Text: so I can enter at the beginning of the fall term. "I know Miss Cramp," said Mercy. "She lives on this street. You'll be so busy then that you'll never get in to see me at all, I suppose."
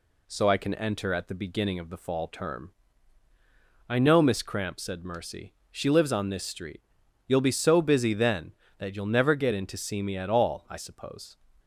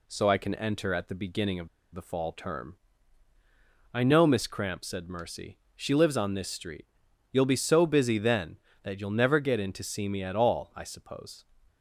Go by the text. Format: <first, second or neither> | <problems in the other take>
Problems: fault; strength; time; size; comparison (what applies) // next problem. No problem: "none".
first | pauses between "of" and "the"; slight; at 1.6 s; 0.25 s long